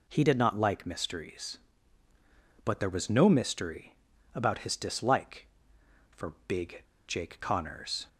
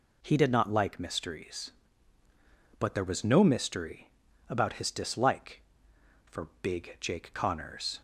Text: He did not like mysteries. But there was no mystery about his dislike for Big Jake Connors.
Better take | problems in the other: second | pauses between "mystery" and "about"; at 3.9 s; 0.40 s long; also in the second // pauses between "Big" and "Jake"; slight; at 6.8 s; 0.25 s long

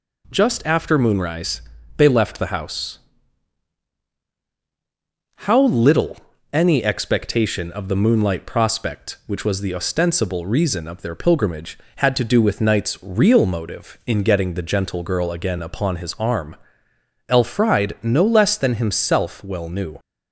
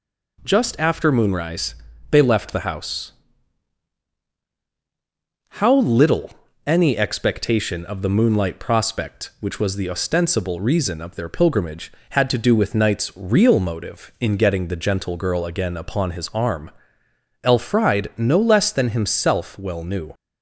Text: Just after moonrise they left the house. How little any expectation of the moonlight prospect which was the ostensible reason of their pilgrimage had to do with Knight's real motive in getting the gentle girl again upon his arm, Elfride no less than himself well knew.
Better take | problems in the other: neither | pauses between "moonrise" and "they"; slight; the same in both // pauses between "little" and "any"; slight; the same in both

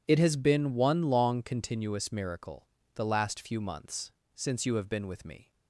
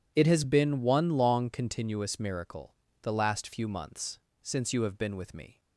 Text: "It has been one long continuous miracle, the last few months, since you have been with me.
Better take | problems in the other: neither | none

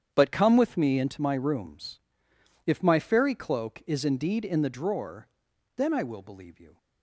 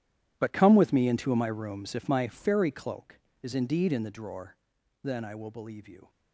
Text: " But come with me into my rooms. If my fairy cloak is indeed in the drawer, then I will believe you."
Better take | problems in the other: first | gets quieter; strong; throughout; 15.5 dB // starts louder than the rest; strong; until 1.3 s; 12 dB; strong in the first

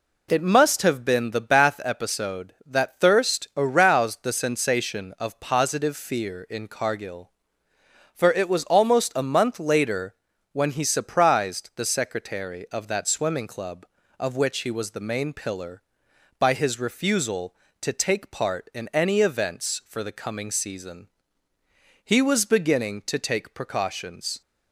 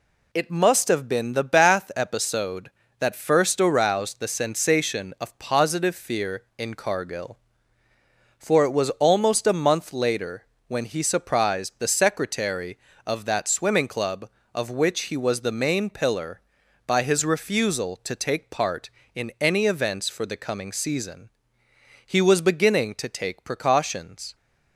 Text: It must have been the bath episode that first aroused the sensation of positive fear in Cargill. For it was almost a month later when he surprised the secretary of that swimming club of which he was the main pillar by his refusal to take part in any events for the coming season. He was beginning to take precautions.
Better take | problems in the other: second | says "thirst" for "first"; at 2.9 s // pauses between "later" and "when"; slight; at 10.1 s; 0.36 s long; slight in the second

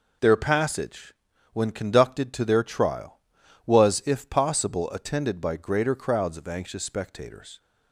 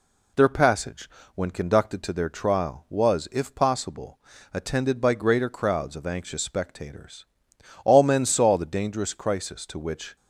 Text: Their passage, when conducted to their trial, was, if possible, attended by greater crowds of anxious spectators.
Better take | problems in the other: first | goes on to say "All men saw the dangerous crisis to which"; strong; from 7.8 s on; 2.3 s long

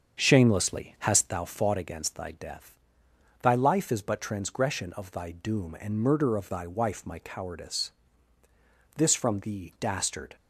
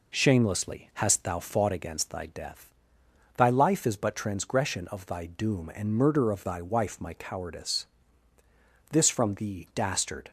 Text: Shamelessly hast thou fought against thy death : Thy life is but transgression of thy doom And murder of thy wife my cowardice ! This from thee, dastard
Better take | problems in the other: second | starts louder than the rest; strong; until 1.4 s; 7 dB

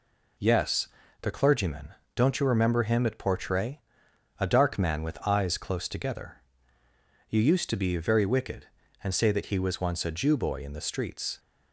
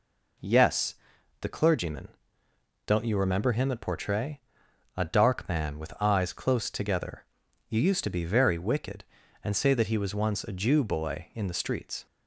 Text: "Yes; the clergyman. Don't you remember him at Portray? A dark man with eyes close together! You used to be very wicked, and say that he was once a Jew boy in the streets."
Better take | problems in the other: neither | none

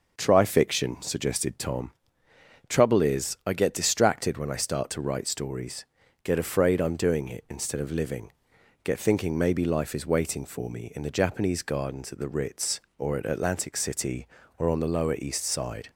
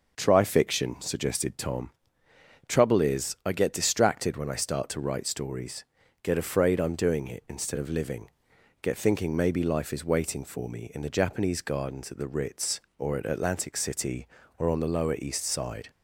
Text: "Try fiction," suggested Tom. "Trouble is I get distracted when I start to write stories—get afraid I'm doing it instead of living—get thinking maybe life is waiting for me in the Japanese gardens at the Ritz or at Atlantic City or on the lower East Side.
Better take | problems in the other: neither | starts louder than the rest; the same in both

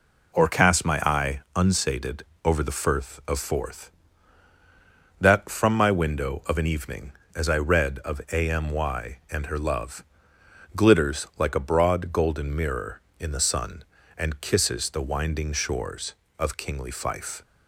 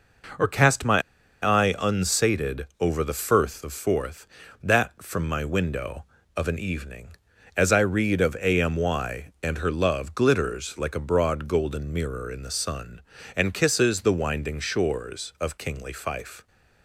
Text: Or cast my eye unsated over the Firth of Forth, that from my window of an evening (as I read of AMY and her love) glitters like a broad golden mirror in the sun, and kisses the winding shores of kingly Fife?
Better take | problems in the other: first | pauses between "my" and "eye"; at 1.0 s; 0.44 s long // pauses between "unsated" and "over"; slight; at 2.6 s; 0.16 s long; slight in the first

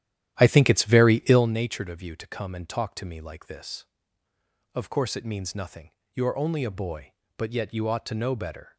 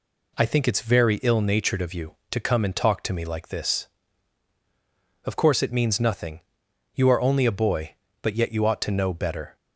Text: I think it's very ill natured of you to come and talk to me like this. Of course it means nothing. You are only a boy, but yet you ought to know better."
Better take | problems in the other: second | starts louder than the rest; strong; until 1.5 s; 12 dB

